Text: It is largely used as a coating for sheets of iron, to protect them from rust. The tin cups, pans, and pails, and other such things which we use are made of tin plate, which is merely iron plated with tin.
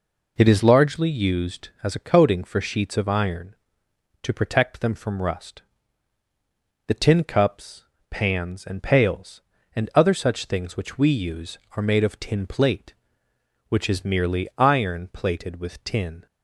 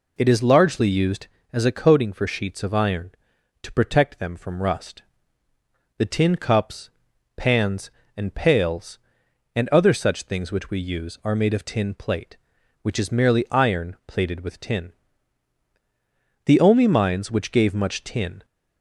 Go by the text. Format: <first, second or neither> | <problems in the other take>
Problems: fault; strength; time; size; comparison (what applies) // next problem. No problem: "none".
first | goes on to say "The only mines which gave much tin"; strong; from 16.4 s on; 2.0 s long